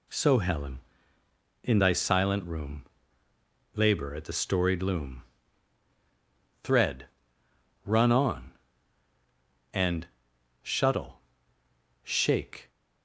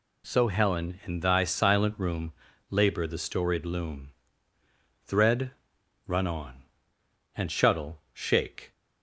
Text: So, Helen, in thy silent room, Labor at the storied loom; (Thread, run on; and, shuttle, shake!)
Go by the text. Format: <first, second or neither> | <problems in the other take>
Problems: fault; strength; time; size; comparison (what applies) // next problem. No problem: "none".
first | skips "at"; at 3.0 s